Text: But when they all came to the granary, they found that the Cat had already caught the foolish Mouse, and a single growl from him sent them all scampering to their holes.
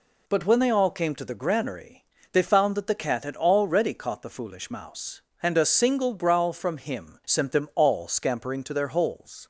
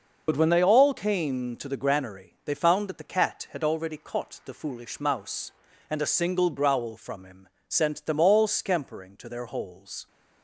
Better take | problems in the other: first | loses the start of "But"; at 0.2 s; 60 ms // pauses between "him" and "sent"; slight; at 7.4 s; 0.18 s long

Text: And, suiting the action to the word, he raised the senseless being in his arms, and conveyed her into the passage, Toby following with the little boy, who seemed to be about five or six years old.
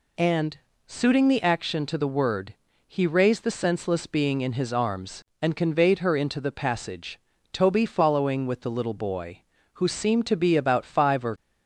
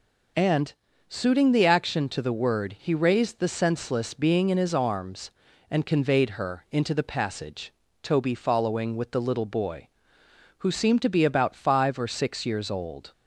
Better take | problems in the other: second | stops before "six years old"; at 11.3 s

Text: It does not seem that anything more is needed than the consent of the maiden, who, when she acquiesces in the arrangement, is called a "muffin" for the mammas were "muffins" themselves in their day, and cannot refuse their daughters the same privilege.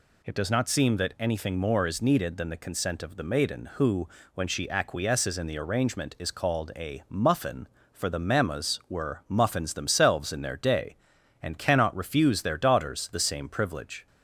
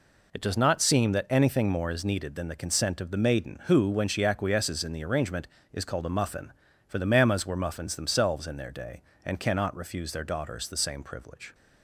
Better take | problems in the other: neither | none

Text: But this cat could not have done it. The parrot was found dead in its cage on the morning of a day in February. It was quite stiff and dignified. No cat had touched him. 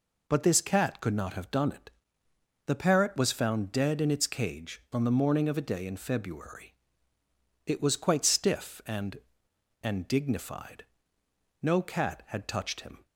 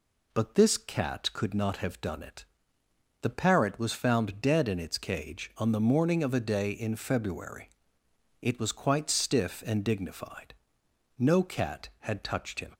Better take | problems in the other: second | says "and" twice; at 9.8 s

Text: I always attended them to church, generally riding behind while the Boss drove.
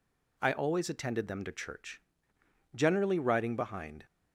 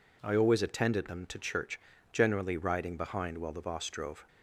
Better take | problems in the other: second | stops before "while the Boss drove"; at 4.0 s

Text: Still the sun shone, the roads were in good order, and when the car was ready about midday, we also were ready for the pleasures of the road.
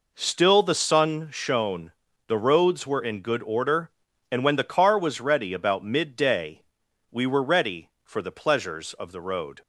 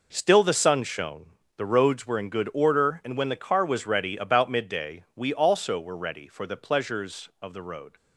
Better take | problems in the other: second | skips "also"; at 7.2 s

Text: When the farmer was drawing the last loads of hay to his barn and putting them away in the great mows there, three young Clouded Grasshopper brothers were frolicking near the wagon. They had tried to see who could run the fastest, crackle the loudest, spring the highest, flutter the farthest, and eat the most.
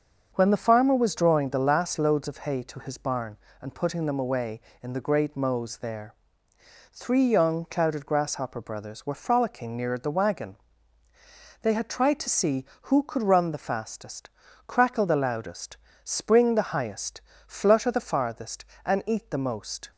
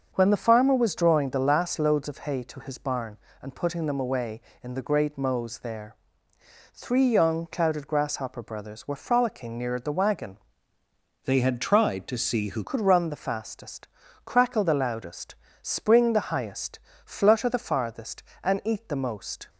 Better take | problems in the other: first | starts louder than the rest; until 1.1 s; 6.5 dB; also in the first // changes voice from "They" to "who"; from 11.2 to 12.6 s; 1.4 s long

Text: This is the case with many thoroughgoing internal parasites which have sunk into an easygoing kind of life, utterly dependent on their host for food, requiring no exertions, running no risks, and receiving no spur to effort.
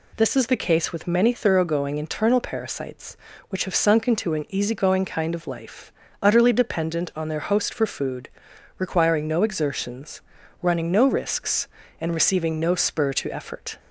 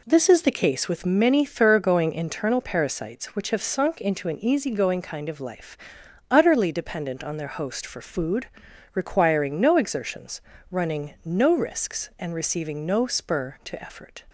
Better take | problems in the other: neither | none

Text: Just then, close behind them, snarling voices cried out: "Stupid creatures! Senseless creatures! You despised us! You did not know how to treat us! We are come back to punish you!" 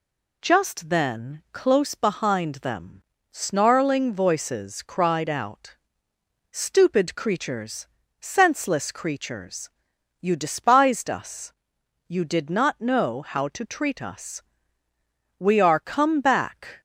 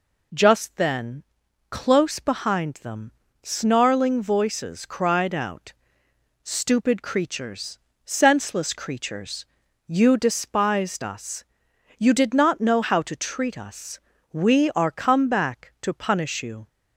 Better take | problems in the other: second | stops before "to punish you"; at 16.7 s

